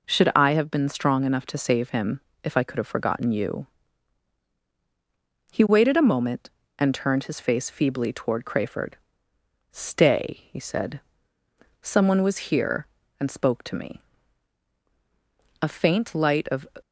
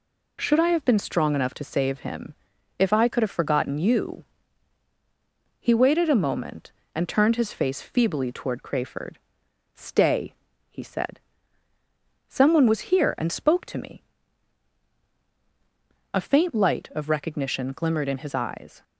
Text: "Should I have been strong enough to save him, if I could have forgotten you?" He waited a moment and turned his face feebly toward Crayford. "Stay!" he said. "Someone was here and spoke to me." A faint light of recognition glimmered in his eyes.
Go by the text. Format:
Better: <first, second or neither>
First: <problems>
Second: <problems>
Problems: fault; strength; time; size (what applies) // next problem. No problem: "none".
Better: second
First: stops before "recognition glimmered in his eyes"; at 16.8 s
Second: none